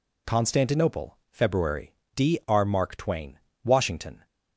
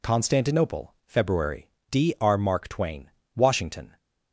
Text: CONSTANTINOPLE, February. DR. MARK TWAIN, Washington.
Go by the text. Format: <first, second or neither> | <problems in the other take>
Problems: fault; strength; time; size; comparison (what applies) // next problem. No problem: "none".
neither | none